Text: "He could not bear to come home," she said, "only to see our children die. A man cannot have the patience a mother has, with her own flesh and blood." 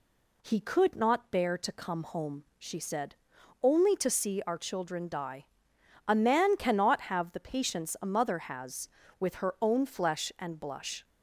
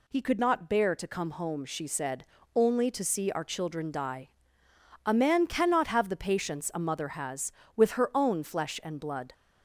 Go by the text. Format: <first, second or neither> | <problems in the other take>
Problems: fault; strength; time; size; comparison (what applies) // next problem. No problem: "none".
second | says "blush" for "blood"; at 10.5 s